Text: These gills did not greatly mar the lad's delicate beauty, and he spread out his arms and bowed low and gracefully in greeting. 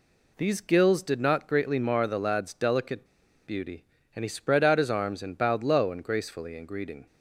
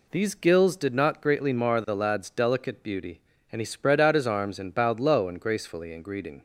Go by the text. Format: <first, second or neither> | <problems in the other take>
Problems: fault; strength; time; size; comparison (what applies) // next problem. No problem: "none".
second | pauses between "delicate" and "beauty"; at 3.0 s; 0.40 s long